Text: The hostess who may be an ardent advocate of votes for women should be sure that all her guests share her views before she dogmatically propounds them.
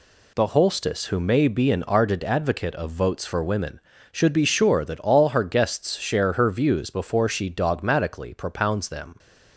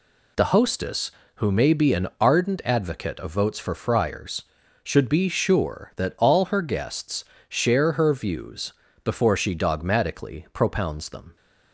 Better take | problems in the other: first | says "friars" for "women"; at 3.7 s // pauses between "guests" and "share"; slight; at 7.2 s; 0.24 s long // pauses between "views" and "before"; slight; at 8.7 s; 0.32 s long

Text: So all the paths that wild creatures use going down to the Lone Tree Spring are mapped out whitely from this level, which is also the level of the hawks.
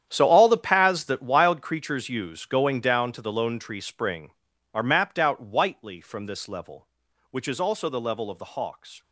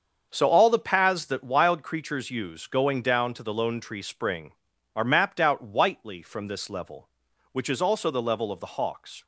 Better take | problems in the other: second | gets quieter; strong; throughout; 15 dB // starts louder than the rest; strong; until 1.1 s; 10 dB; also in the second

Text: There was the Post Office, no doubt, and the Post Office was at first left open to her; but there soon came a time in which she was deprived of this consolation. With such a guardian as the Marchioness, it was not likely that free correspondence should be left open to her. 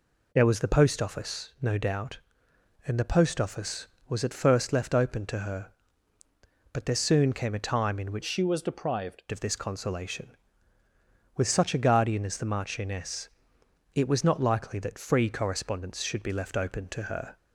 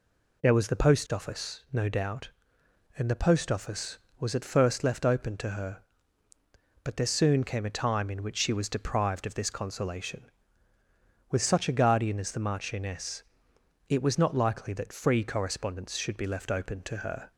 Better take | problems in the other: second | changes voice from "she" to "deprived"; from 8.2 to 9.2 s; 1.0 s long

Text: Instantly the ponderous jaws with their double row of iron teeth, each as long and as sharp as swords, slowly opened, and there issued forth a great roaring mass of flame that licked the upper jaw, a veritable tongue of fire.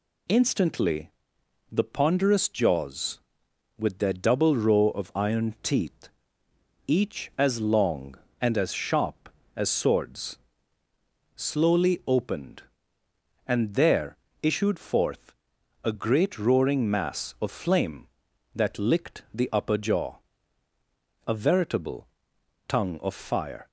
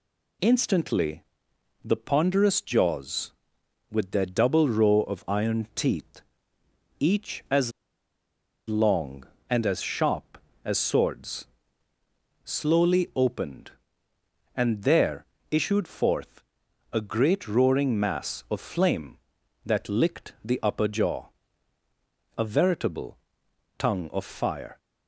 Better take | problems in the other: first | pauses between "Instantly" and "the"; noticeable; at 1.2 s; 0.62 s long; noticeable in the first // pauses between "as" and "long"; at 7.7 s; 0.98 s long // pauses between "there" and "issued"; slight; at 15.2 s; 0.26 s long; slight in the first // pauses between "forth" and "a"; noticeable; at 16.4 s; 0.52 s long; noticeable in the first // pauses between "veritable" and "tongue"; noticeable; at 23.1 s; 0.60 s long; noticeable in the first

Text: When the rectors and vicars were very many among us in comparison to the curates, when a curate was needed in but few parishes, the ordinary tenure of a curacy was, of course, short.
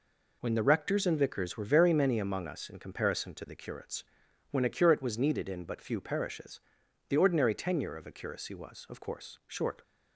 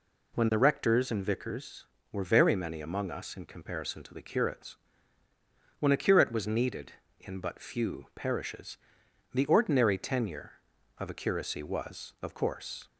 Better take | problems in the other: first | stops before "short"; at 12.8 s

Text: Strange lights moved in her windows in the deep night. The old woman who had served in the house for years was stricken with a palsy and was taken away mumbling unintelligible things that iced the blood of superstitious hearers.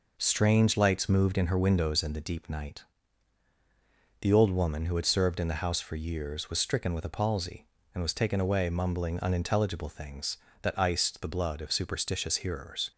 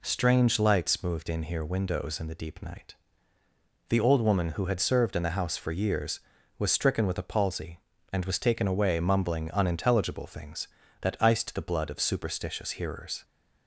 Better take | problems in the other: first | says "here" for "her"; at 1.4 s

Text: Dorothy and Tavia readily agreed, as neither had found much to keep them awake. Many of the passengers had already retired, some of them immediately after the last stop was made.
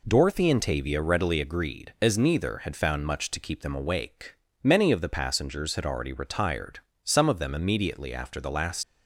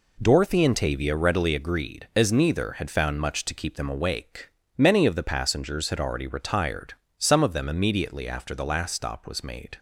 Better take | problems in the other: second | stops before "stop was made"; at 8.8 s

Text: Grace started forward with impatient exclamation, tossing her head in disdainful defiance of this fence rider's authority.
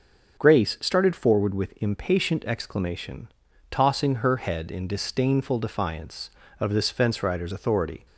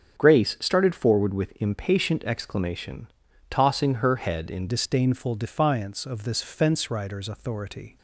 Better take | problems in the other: first | starts louder than the rest; strong; until 1.2 s; 8 dB; also in the first // changes voice at "disdainful"; from 4.6 s on; 3.3 s long

